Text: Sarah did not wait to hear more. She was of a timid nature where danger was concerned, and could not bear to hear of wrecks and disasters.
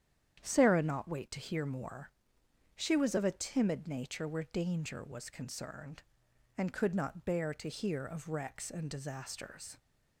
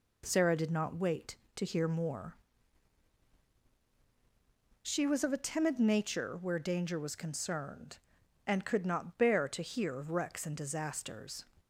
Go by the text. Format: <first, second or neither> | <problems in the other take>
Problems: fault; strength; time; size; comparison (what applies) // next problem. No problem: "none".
second | starts louder than the rest; strong; until 1.4 s; 9 dB // skips "did"; at 0.8 s